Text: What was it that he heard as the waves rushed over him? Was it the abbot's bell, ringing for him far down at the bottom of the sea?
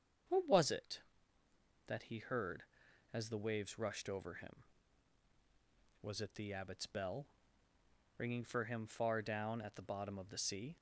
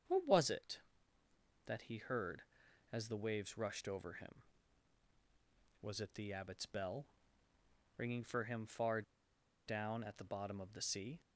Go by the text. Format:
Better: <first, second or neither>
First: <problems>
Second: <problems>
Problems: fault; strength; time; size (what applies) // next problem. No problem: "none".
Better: first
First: starts louder than the rest; until 2.1 s; 7 dB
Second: starts louder than the rest; until 1.9 s; 7 dB // pauses between "far" and "down"; noticeable; at 9.0 s; 0.65 s long